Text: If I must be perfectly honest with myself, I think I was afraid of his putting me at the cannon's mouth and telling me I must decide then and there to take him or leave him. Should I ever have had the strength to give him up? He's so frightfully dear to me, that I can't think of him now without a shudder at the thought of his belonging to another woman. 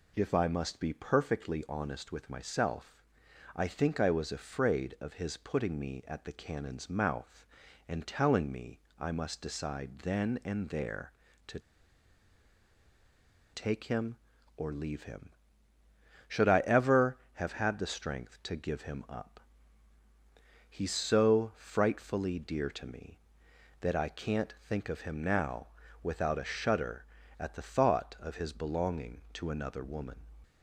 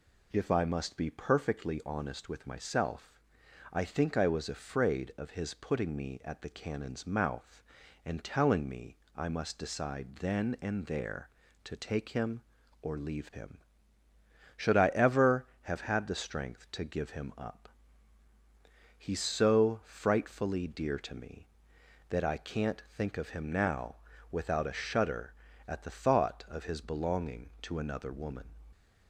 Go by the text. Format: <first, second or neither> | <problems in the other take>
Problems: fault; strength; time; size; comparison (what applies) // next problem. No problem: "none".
second | pauses between "me" and "I"; slight; at 8.7 s; 0.20 s long; slight in the second // pauses between "to" and "take"; strong; at 11.5 s; 1.9 s long // pauses between "now" and "without"; slight; at 25.6 s; 0.34 s long; slight in the second